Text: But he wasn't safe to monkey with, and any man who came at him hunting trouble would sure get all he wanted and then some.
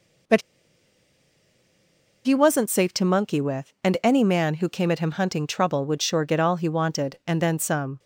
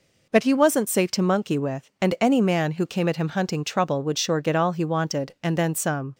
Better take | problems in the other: second | pauses between "But" and "he"; strong; at 0.4 s; 1.8 s long

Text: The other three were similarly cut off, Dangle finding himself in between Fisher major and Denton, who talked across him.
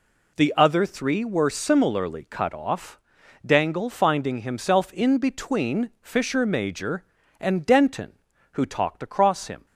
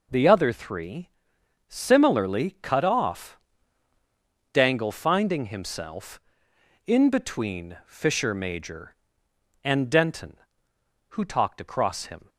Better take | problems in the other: first | skips "were"; at 1.3 s

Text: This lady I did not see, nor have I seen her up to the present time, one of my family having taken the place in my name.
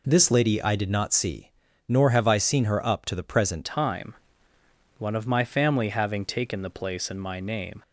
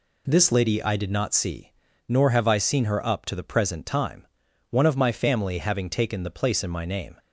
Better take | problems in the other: second | changes voice at "time"; from 3.6 s on; 4.2 s long

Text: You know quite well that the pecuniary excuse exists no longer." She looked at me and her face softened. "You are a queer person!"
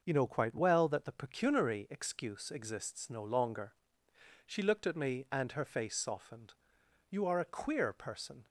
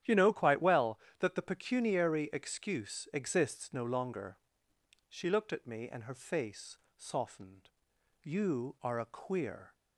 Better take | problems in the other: first | starts louder than the rest; strong; until 1.2 s; 10.5 dB // pauses between "face" and "softened"; slight; at 6.7 s; 0.18 s long // stops before "person"; at 9.7 s

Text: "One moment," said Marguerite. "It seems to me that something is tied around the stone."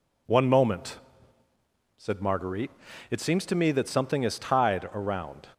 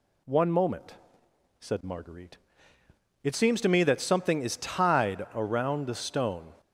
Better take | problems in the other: second | stops before "the stone"; at 5.5 s

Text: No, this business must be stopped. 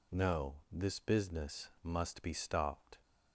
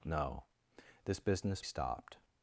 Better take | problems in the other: first | skips "must be"; at 1.6 s

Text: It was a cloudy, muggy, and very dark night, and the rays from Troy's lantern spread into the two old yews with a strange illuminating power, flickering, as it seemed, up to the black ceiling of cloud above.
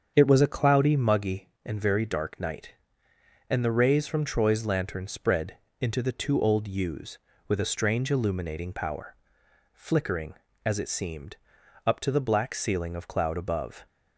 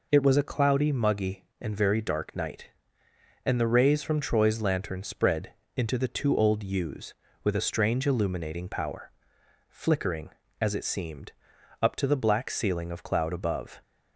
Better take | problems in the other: second | starts louder than the rest; strong; until 1.3 s; 7.5 dB // pauses between "spread" and "into"; slight; at 5.5 s; 0.24 s long; slight in the second

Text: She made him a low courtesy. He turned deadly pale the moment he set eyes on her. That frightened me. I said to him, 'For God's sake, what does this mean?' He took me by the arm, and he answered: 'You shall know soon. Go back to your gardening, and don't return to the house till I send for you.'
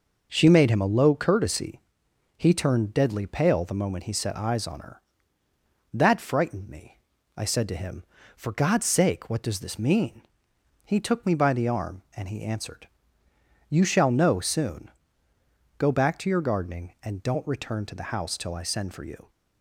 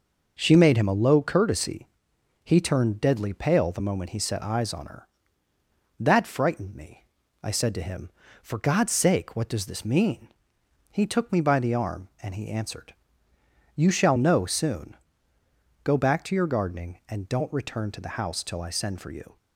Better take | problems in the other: neither | none

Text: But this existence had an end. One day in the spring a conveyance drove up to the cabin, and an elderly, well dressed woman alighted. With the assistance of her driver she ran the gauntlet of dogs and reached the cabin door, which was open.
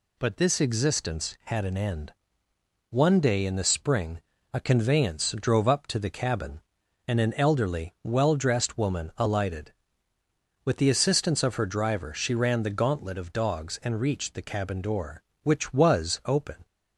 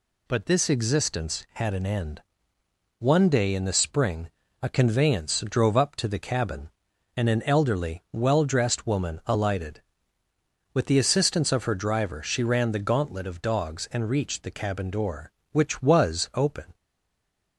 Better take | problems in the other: first | pauses between "spring" and "a"; slight; at 4.3 s; 0.32 s long; slight in the first // stays silent after the last word; slight; from 16.7 s on; 0.8 s long

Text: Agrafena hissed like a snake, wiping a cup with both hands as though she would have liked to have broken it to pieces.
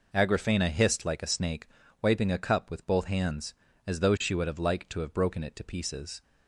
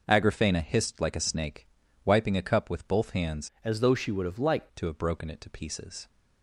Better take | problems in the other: first | changes voice from "as" to "liked"; from 3.6 to 4.6 s; 1.0 s long

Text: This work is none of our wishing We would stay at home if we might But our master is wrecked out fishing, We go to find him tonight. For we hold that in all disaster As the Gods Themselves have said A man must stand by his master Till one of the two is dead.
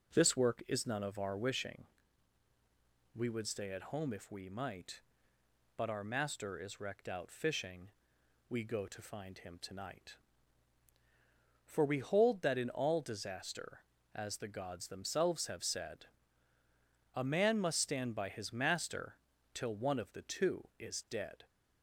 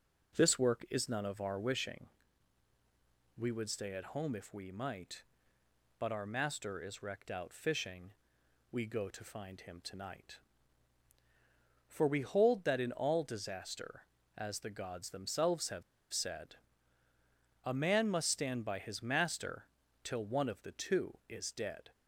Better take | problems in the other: first | pauses between "wishing" and "We"; strong; at 2.0 s; 1.2 s long; strong in the first // pauses between "have" and "said"; slight; at 15.8 s; 0.30 s long // pauses between "said" and "A"; at 16.5 s; 1.0 s long; also in the first // pauses between "master" and "Till"; at 19.6 s; 0.38 s long; also in the first

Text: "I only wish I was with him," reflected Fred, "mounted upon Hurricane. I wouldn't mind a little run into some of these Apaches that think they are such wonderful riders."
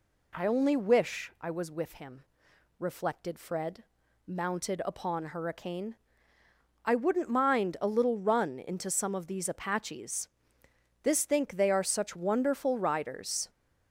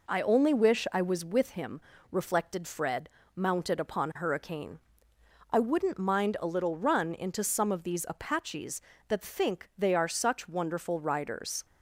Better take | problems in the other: second | says "this" for "that"; at 11.0 s

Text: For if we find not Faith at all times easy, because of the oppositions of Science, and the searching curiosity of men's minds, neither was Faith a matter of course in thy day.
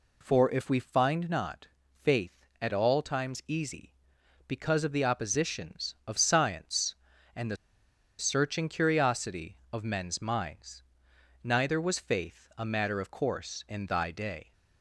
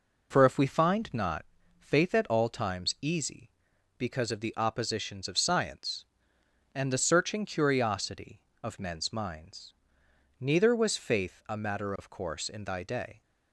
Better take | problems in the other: second | pauses between "not" and "Faith"; at 1.6 s; 0.38 s long; slight in the second // pauses between "the" and "searching"; noticeable; at 7.5 s; 0.63 s long

